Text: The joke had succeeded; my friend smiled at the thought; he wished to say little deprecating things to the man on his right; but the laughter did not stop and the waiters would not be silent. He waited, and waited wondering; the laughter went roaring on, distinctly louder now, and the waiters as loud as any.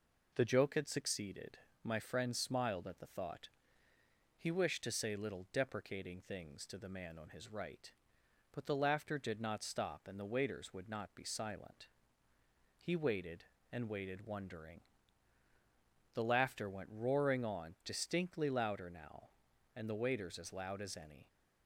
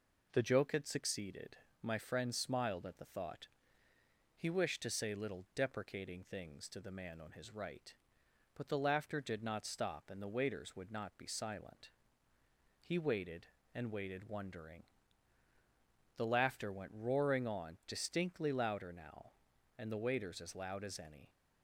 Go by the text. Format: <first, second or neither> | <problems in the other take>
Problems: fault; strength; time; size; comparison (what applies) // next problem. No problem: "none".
neither | none